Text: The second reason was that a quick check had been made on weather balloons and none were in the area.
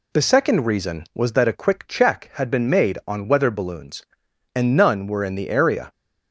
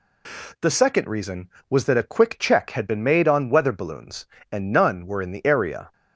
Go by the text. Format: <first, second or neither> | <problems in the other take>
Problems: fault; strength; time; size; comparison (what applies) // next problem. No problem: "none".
neither | none